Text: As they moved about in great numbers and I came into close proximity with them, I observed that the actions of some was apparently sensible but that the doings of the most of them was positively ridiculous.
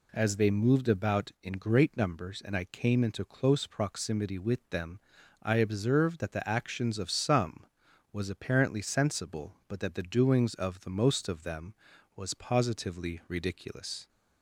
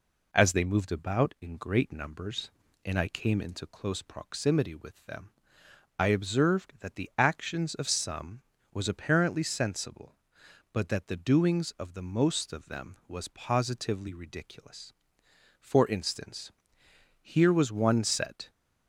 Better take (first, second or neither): first